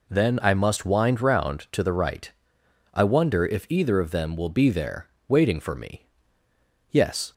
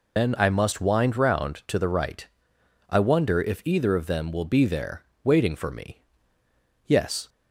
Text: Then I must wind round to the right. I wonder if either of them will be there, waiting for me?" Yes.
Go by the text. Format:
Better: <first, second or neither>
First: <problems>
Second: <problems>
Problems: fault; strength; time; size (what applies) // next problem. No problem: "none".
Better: first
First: none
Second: loses the start of "Then"; at 0.1 s; 115 ms